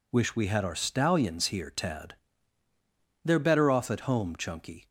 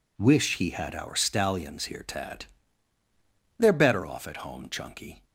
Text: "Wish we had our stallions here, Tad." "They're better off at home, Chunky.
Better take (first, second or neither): first